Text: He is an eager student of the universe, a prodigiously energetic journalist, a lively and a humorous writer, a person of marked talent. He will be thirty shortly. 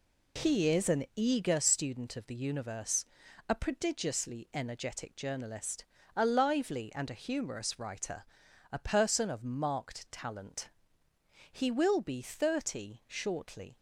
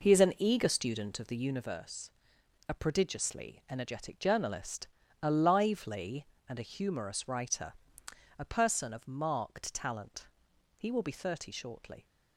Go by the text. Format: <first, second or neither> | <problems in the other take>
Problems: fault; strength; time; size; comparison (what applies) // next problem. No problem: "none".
first | starts louder than the rest; noticeable; until 1.8 s; 5 dB